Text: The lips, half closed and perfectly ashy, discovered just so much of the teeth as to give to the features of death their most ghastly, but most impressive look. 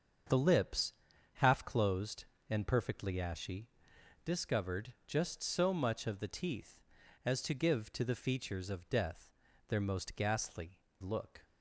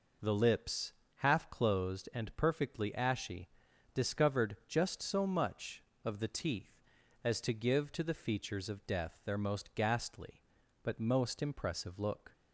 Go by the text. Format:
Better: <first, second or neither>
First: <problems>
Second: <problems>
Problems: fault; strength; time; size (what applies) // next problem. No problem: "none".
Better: second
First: starts louder than the rest; until 1.7 s; 6.5 dB // pauses between "death" and "their"; at 9.2 s; 0.40 s long // skips "but most impressive"; at 10.9 s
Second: none